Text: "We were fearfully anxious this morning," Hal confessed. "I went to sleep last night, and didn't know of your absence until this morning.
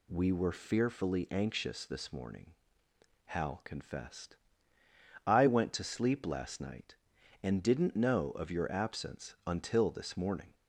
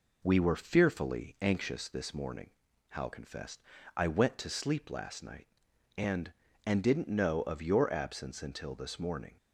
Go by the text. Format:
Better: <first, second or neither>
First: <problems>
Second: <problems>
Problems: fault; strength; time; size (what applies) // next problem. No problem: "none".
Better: first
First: none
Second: says "and" twice; at 6.6 s